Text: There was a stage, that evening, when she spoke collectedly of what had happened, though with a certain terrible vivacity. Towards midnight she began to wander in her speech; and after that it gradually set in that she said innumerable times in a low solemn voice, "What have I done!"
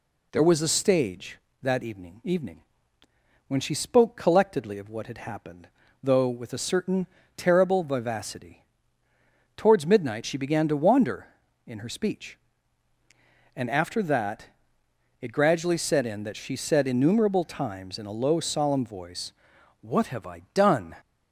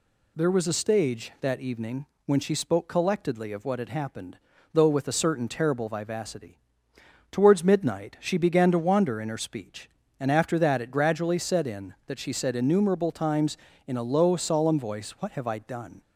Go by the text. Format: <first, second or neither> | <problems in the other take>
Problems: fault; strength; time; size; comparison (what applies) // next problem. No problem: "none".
second | says "evening" twice; at 2.2 s // pauses between "certain" and "terrible"; slight; at 7.0 s; 0.28 s long // pauses between "that" and "it"; noticeable; at 14.4 s; 0.74 s long